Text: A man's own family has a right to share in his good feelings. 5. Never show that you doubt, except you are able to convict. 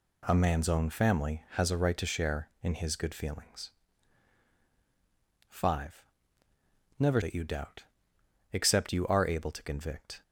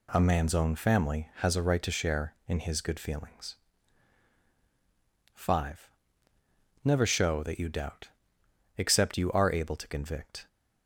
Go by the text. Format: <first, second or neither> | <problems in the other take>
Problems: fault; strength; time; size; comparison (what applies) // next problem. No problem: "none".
second | skips "show"; at 7.2 s